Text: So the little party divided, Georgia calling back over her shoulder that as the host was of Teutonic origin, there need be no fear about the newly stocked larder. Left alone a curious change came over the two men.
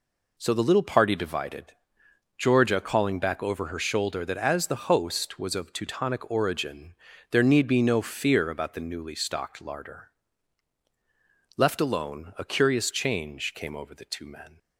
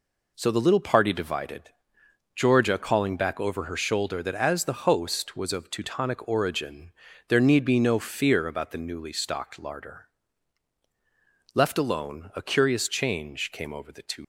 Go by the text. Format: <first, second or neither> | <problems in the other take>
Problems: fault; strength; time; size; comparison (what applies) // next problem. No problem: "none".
first | stops before "men"; at 14.2 s